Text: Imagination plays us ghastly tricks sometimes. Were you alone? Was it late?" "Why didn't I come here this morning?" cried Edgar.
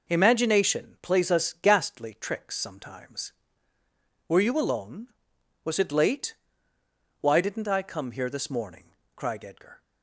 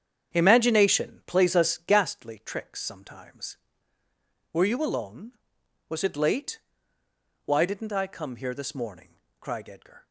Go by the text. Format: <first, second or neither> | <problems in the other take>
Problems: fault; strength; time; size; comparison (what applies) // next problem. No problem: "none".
first | starts louder than the rest; strong; until 2.0 s; 8 dB